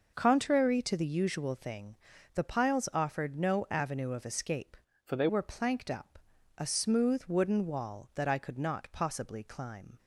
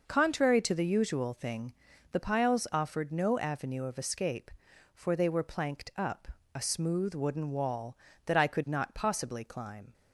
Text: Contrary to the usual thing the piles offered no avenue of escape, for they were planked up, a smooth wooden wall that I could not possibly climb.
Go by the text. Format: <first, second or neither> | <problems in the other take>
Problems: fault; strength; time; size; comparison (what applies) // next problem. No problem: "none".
second | pauses between "thing" and "the"; at 1.9 s; 0.38 s long; also in the second // changes voice from "for" to "they"; from 5.0 to 5.2 s; 0.2 s long